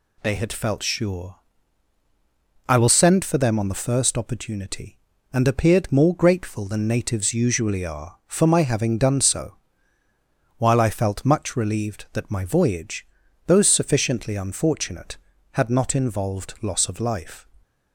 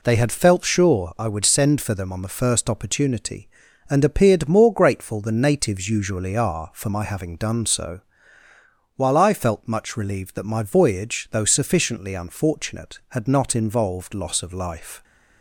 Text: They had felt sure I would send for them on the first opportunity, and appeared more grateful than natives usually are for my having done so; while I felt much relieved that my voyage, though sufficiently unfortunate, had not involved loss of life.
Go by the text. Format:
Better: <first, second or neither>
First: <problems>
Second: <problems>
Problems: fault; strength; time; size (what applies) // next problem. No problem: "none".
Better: second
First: pauses between "sure" and "I"; strong; at 1.3 s; 1.3 s long // says "will" for "would"; at 2.7 s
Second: none